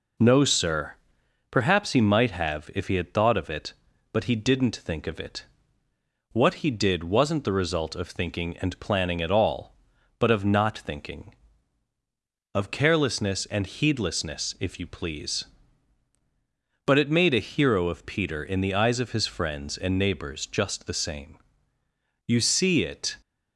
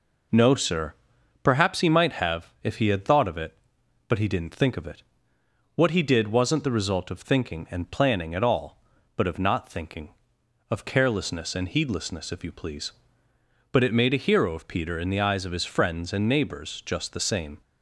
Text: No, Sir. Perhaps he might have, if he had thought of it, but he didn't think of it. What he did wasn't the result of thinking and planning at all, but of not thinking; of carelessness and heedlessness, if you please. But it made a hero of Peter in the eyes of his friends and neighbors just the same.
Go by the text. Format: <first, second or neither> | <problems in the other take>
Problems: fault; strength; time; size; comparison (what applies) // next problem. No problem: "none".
second | goes on to say "You see it"; noticeable; from 22.2 s on; 0.92 s long